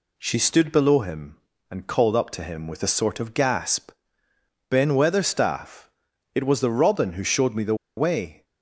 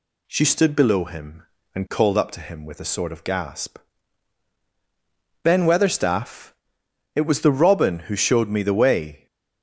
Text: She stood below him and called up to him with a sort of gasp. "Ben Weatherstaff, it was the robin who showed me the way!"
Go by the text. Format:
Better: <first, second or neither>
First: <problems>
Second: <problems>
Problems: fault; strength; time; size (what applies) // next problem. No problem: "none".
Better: second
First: pauses between "the" and "way"; slight; at 7.7 s; 0.22 s long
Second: none